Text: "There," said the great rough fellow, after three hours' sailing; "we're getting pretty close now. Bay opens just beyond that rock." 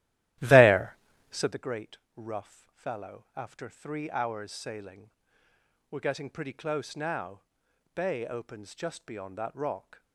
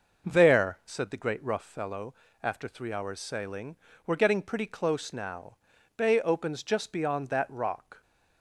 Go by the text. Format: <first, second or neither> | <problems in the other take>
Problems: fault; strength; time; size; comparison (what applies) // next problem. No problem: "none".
second | starts louder than the rest; strong; until 1.5 s; 14.5 dB // pauses between "great" and "rough"; slight; at 1.9 s; 0.18 s long